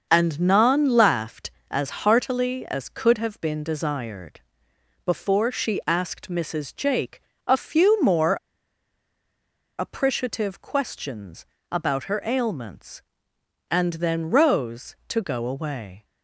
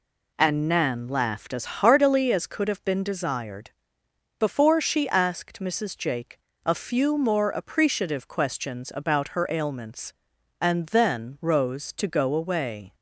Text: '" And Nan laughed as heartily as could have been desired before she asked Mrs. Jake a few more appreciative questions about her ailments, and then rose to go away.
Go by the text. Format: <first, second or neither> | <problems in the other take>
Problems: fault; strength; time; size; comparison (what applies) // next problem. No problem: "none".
second | starts louder than the rest; until 1.0 s; 6.5 dB // pauses between "desired" and "before"; noticeable; at 4.4 s; 0.64 s long; noticeable in the second // pauses between "Jake" and "a"; slight; at 7.2 s; 0.24 s long; slight in the second // pauses between "more" and "appreciative"; strong; at 8.3 s; 1.4 s long // pauses between "questions" and "about"; slight; at 11.4 s; 0.24 s long